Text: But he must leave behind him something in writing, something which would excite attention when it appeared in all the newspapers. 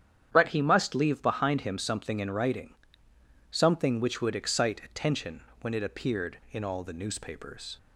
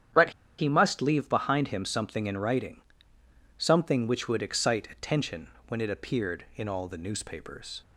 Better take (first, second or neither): first